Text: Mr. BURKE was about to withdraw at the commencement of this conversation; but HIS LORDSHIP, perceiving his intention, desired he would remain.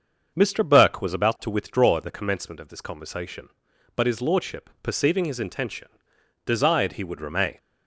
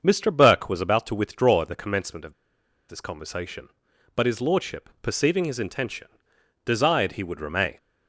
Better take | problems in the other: first | starts louder than the rest; until 1.0 s; 6.5 dB; also in the first // pauses between "of" and "this"; noticeable; at 2.3 s; 0.55 s long

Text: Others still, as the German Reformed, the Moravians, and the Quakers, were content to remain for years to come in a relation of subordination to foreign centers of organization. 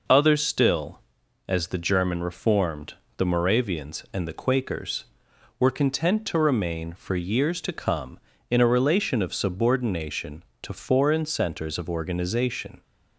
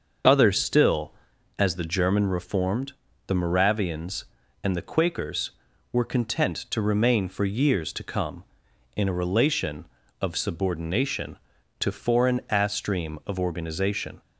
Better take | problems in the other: first | starts louder than the rest; until 1.6 s; 6.5 dB // says "astream" for "centers"; at 12.4 s

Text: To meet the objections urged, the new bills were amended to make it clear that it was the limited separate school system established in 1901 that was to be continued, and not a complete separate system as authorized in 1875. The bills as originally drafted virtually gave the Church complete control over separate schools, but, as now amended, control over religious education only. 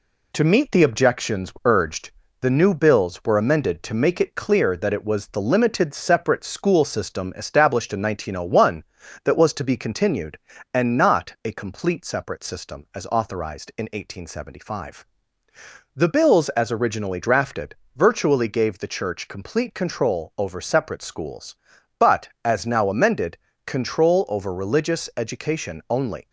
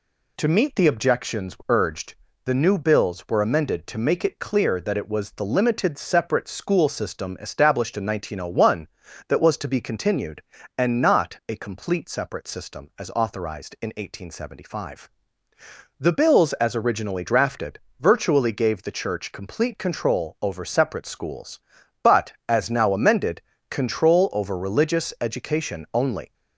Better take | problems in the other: second | gets quieter; slight; throughout; 2.5 dB // pauses between "drafted" and "virtually"; slight; at 17.7 s; 0.22 s long; slight in the second

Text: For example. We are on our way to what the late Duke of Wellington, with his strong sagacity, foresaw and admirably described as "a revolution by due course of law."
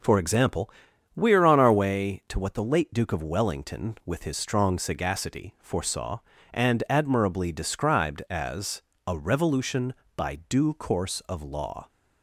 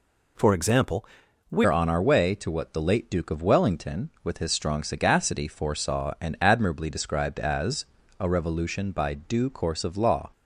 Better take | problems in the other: first | changes voice at "are"; from 1.6 s on; 8.7 s long // pauses between "as" and "a"; slight; at 7.8 s; 0.34 s long; slight in the first

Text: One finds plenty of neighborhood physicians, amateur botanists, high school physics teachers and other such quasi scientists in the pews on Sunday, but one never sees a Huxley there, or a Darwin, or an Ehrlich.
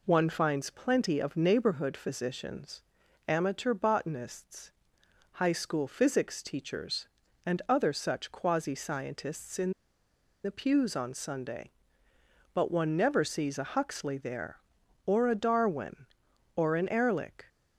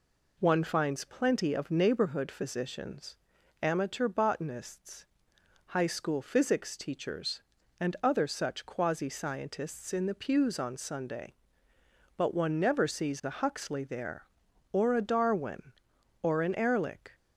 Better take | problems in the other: second | pauses between "in" and "the"; noticeable; at 9.7 s; 0.71 s long

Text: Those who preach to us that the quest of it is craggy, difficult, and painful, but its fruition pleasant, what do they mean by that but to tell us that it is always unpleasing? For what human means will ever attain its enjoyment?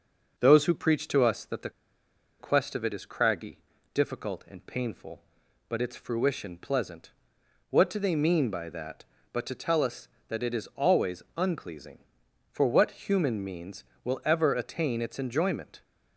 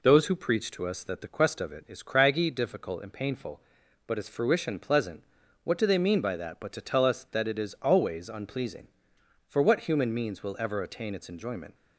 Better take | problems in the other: second | pauses between "the" and "quest"; noticeable; at 1.7 s; 0.69 s long

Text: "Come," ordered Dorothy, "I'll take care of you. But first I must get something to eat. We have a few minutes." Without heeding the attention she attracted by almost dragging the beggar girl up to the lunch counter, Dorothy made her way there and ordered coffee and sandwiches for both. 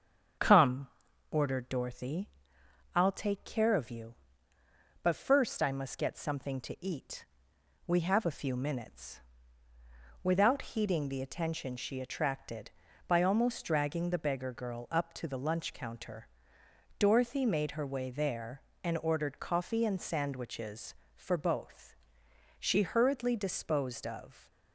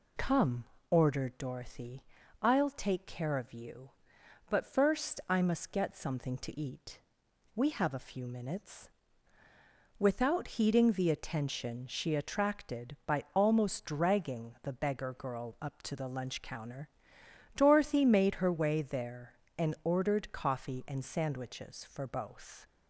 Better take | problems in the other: second | starts louder than the rest; strong; until 1.8 s; 7.5 dB // goes on to say "She hurriedly disposed of"; strong; from 22.5 s on; 1.9 s long

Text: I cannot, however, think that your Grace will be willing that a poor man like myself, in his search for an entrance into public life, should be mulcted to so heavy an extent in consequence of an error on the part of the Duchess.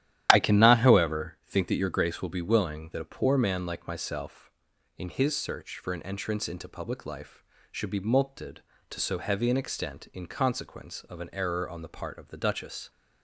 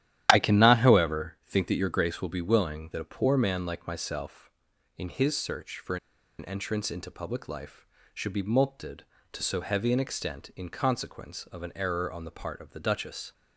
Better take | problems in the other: first | starts louder than the rest; strong; until 1.3 s; 11 dB; strong in the first // pauses between "for" and "an"; at 5.9 s; 0.42 s long

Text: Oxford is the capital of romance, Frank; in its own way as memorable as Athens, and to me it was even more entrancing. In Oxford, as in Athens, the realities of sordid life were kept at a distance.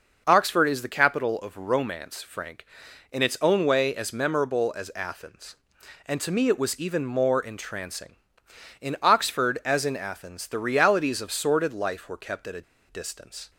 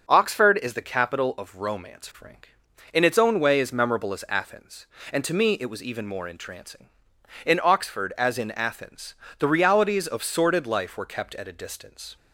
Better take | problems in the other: second | pauses between "a" and "distance"; slight; at 12.6 s; 0.26 s long

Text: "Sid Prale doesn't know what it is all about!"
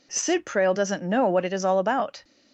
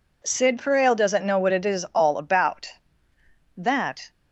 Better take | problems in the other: first | goes on to say "That"; from 3.5 s on; 0.54 s long

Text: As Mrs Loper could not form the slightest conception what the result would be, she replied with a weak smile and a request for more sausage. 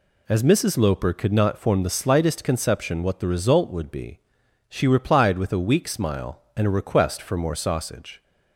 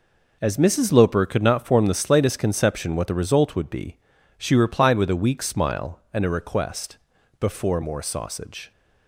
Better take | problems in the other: first | says "before" for "for"; at 7.3 s

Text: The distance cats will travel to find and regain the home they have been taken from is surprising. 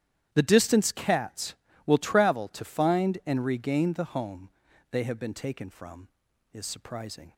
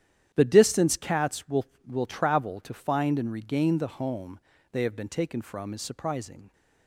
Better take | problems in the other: first | starts louder than the rest; strong; until 1.3 s; 10.5 dB; strong in the first // says "will" twice; at 1.8 s // pauses between "home" and "they"; slight; at 4.4 s; 0.32 s long; also in the first

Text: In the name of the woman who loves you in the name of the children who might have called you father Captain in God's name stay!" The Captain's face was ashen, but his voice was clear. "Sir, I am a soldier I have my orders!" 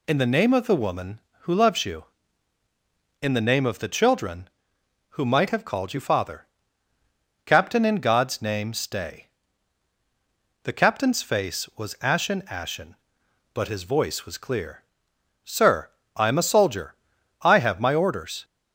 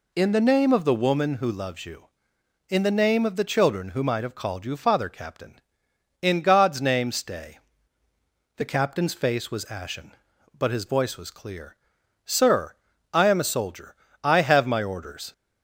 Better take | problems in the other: second | pauses between "father" and "Captain"; at 6.4 s; 1.0 s long // says "ashen" twice; at 12.5 s // pauses between "soldier" and "I"; at 16.9 s; 0.44 s long; slight in the second

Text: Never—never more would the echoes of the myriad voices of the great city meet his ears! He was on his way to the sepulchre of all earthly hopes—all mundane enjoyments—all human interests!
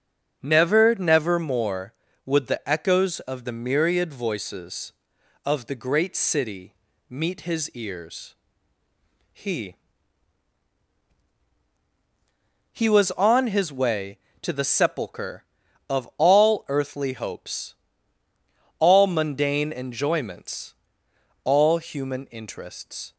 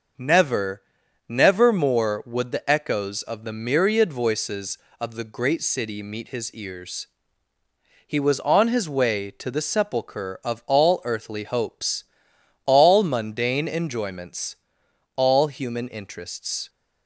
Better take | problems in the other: second | starts louder than the rest; until 1.4 s; 6.5 dB // pauses between "city" and "meet"; slight; at 6.7 s; 0.36 s long // says "He" twice; at 12.7 s

